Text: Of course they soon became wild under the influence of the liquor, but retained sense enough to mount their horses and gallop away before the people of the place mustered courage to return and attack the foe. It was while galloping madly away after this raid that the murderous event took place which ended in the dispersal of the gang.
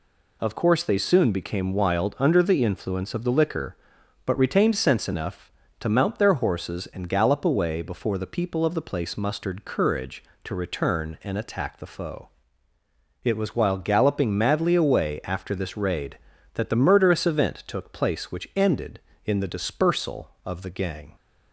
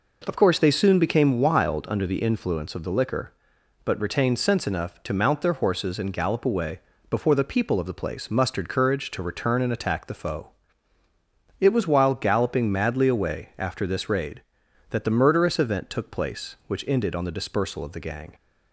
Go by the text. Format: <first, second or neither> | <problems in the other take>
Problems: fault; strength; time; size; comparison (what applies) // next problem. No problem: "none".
first | pauses between "away" and "before"; slight; at 6.7 s; 0.32 s long // says "on" for "in"; at 17.1 s